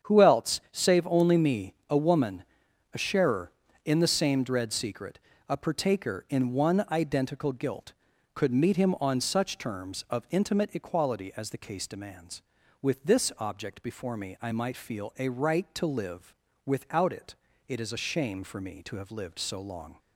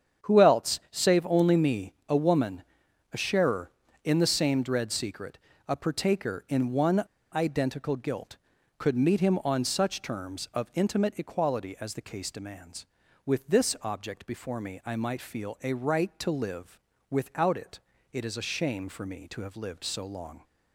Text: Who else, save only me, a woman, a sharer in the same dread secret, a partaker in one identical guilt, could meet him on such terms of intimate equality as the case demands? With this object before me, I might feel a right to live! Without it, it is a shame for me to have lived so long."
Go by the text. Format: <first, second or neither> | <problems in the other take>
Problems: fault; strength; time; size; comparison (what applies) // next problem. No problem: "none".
first | starts louder than the rest; strong; until 1.3 s; 8 dB; strong in the first // pauses between "one" and "identical"; slight; at 7.0 s; 0.30 s long